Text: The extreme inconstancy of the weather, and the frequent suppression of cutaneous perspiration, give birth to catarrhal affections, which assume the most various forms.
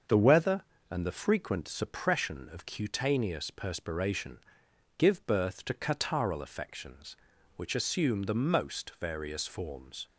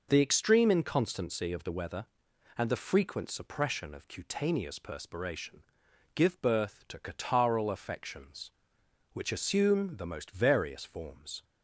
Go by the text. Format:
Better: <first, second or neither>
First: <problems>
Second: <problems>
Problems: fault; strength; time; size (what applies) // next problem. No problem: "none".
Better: second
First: starts louder than the rest; until 1.3 s; 6.5 dB // skips "extreme inconstancy of the"; at 0.1 s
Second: none